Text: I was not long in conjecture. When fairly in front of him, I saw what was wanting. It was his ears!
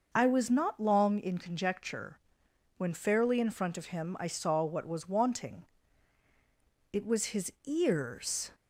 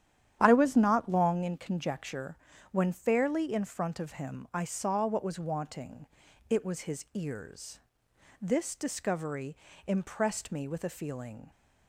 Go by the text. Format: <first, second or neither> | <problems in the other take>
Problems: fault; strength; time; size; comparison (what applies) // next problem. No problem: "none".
first | starts louder than the rest; strong; until 1.4 s; 10 dB // goes on to say "This discovery impressed me with a feeling"; strong; from 8.4 s on; 3.1 s long